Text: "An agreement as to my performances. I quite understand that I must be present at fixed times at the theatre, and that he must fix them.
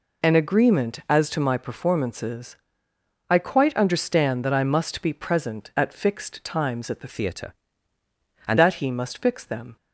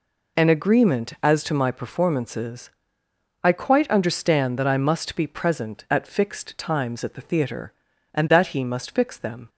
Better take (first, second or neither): second